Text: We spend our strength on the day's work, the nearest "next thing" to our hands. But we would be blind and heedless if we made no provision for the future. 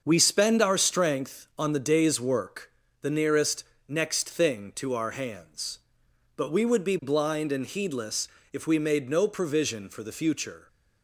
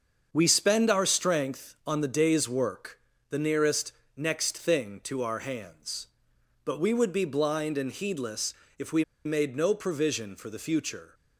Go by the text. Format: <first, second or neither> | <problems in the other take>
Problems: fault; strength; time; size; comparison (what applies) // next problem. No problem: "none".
first | starts louder than the rest; until 1.3 s; 6.5 dB; also in the first // pauses between "nearest" and "next"; slight; at 3.9 s; 0.24 s long; slight in the first // pauses between "heedless" and "if"; slight; at 8.5 s; 0.26 s long; slight in the first // pauses between "we" and "made"; slight; at 9.0 s; 0.22 s long